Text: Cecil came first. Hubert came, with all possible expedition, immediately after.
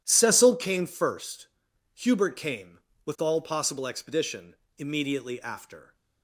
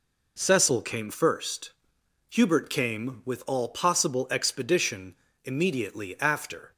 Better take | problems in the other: neither | none

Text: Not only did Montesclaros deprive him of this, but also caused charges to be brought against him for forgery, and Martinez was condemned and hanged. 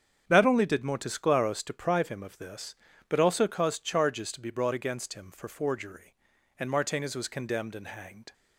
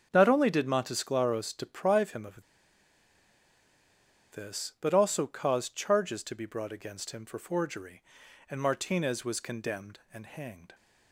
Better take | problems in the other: first | starts louder than the rest; strong; until 1.1 s; 8 dB; strong in the first // pauses between "of" and "this"; strong; at 2.4 s; 1.8 s long

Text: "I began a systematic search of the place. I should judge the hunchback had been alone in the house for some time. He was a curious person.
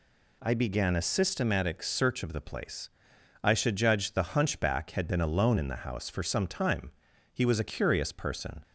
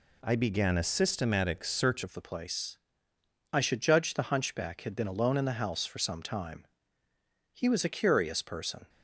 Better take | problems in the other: first | changes voice at "of"; from 2.0 s on; 6.8 s long

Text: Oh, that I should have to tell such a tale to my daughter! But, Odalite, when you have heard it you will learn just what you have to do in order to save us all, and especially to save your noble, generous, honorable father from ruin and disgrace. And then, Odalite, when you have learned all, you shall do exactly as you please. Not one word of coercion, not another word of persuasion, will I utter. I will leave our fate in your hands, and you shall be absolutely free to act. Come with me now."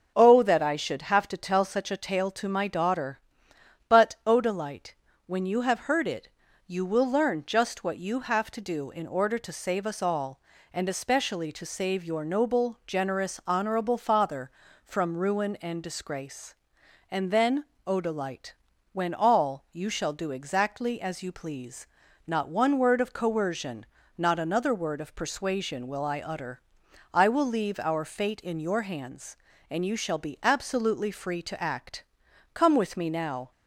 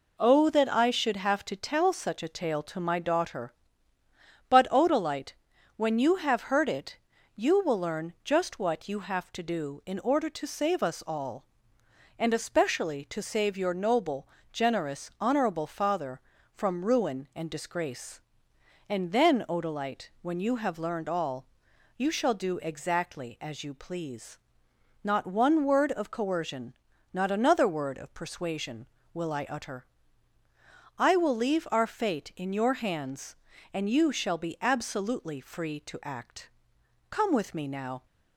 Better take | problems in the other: second | pauses between "it" and "you"; at 6.2 s; 0.40 s long; also in the second // skips "you have learned"; at 19.1 s

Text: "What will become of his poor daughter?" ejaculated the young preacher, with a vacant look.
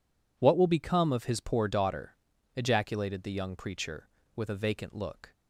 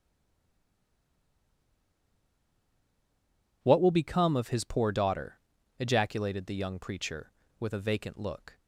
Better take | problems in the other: first | stays silent before the first word; strong; until 3.6 s; 3.6 s long

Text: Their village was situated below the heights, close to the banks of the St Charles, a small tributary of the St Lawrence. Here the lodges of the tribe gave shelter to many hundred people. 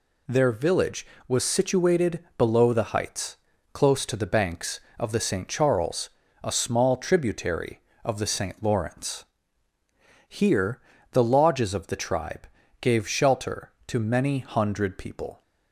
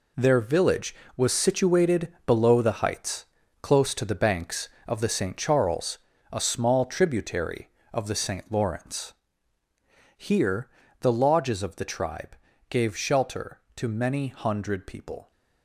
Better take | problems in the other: first | gets quieter; strong; throughout; 10.5 dB // pauses between "Here" and "the"; slight; at 10.6 s; 0.32 s long; slight in the first // pauses between "tribe" and "gave"; slight; at 12.3 s; 0.32 s long; slight in the first

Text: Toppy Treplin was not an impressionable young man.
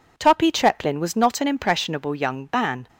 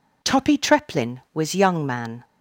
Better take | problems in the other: first | skips "not an impressionable"; at 1.5 s

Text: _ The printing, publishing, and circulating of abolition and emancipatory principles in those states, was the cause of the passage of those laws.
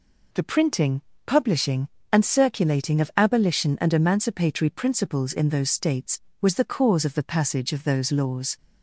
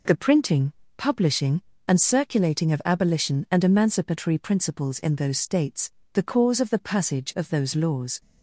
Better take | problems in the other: first | skips "was"; at 6.0 s

